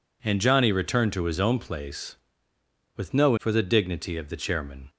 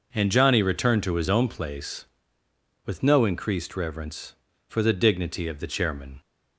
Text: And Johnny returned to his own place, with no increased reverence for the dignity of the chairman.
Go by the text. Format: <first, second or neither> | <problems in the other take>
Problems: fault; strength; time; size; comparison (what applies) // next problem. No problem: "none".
second | skips "increased reverence"; at 3.3 s